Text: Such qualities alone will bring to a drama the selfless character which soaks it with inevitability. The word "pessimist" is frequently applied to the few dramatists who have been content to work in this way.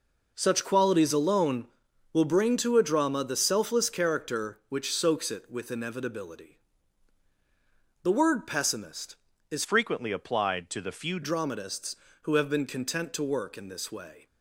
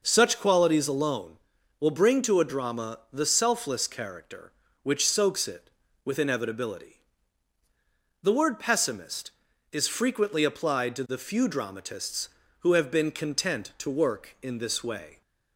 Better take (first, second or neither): second